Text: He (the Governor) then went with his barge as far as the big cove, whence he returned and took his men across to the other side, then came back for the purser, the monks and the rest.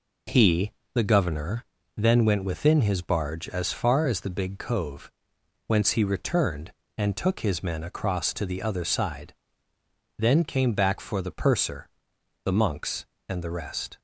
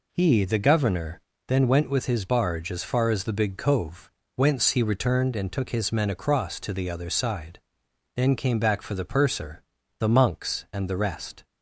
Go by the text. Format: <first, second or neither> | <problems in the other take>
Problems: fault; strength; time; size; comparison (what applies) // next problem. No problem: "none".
second | says "within" for "with"; at 2.4 s